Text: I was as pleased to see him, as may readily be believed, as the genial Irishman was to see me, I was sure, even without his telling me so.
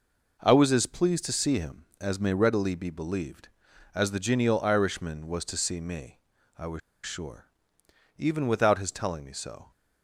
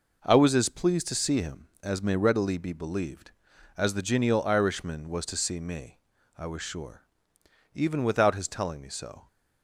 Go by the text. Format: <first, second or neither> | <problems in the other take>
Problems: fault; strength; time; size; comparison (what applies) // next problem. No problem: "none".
second | pauses between "was" and "sure"; slight; at 6.8 s; 0.26 s long